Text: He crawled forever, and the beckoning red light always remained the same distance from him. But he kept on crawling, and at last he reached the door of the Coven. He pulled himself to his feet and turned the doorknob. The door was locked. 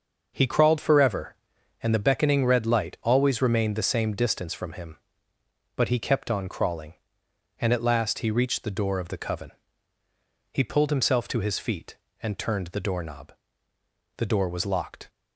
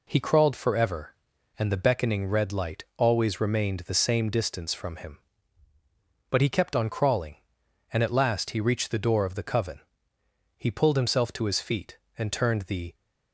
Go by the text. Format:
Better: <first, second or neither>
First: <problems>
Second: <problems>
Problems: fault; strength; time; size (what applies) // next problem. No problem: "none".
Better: first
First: none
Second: stops before "doorknob The door was locked"; at 12.9 s